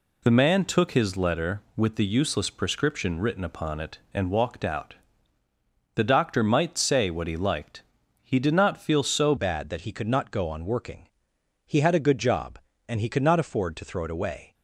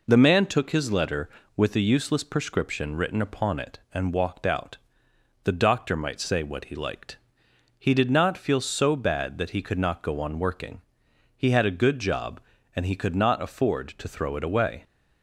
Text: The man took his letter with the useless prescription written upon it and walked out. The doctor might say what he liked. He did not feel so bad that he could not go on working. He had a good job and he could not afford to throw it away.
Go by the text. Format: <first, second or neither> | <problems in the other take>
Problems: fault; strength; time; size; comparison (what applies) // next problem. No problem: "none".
second | changes voice at "bad"; from 9.3 s on; 5.2 s long